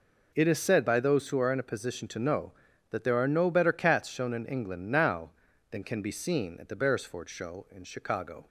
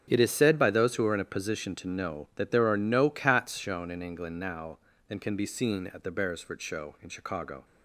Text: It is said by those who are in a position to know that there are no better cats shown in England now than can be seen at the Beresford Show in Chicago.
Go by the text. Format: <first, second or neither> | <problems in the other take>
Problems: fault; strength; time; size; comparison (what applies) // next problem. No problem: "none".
first | starts louder than the rest; strong; until 1.0 s; 7.5 dB // skips "better"; at 3.1 s